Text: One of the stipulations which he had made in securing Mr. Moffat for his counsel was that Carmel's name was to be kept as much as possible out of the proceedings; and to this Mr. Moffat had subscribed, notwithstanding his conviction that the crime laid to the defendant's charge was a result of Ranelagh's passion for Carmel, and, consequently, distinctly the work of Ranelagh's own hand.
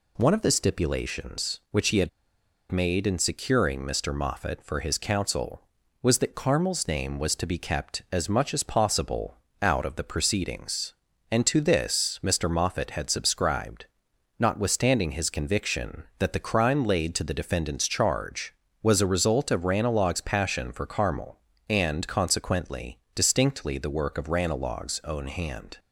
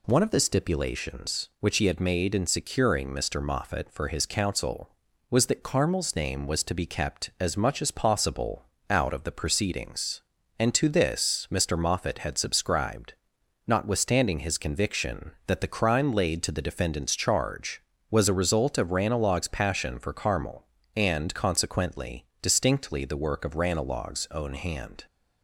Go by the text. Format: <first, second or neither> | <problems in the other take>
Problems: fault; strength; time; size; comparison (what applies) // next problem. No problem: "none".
second | pauses between "had" and "made"; noticeable; at 2.0 s; 0.62 s long // pauses between "possible" and "out"; slight; at 9.3 s; 0.24 s long; slight in the second